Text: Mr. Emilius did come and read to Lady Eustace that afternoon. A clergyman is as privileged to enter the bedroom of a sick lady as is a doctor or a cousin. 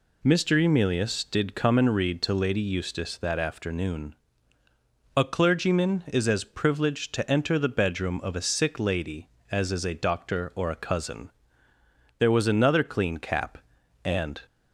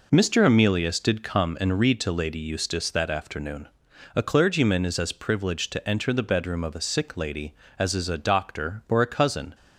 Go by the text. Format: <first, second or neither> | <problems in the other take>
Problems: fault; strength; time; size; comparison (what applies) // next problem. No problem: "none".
second | goes on to say "There was another clean cap and"; strong; from 12.1 s on; 2.2 s long